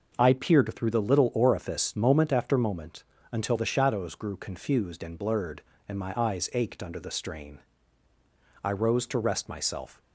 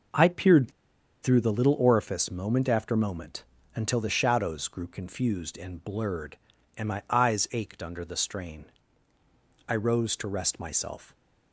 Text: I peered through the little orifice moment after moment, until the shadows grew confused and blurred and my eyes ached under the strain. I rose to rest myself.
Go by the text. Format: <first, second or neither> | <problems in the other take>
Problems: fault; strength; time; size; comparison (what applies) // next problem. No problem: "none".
first | pauses between "peered" and "through"; noticeable; at 0.7 s; 0.52 s long